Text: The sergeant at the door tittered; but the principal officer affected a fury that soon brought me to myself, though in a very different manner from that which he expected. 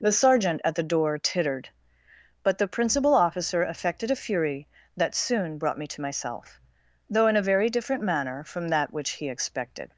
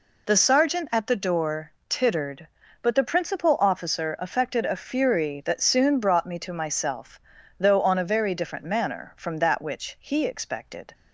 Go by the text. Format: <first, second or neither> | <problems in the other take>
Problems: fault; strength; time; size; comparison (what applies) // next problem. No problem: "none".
first | pauses between "door" and "tittered"; slight; at 1.7 s; 0.18 s long // says "on" for "in"; at 7.8 s